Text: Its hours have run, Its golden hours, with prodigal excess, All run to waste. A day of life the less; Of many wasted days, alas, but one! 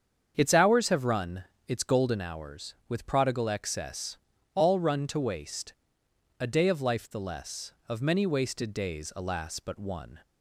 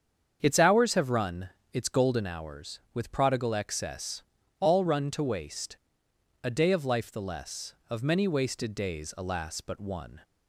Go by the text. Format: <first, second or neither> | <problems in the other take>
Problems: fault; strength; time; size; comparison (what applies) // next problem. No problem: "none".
neither | starts louder than the rest; strong; the same in both